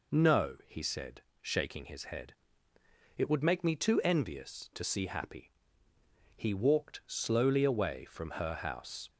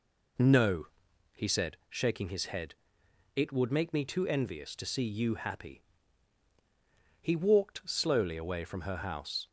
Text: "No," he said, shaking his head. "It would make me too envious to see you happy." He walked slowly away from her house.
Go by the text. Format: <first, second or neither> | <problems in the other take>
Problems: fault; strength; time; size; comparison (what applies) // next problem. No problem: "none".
second | skips "you"; at 5.0 s